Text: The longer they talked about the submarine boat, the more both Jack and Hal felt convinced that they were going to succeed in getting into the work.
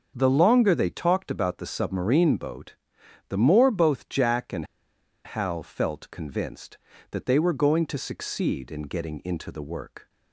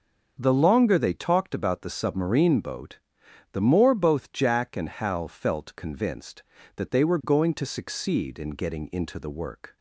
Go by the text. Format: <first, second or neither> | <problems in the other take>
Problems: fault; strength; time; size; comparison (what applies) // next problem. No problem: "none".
second | starts louder than the rest; until 1.1 s; 6.5 dB; also in the second // pauses between "and" and "Hal"; noticeable; at 4.6 s; 0.60 s long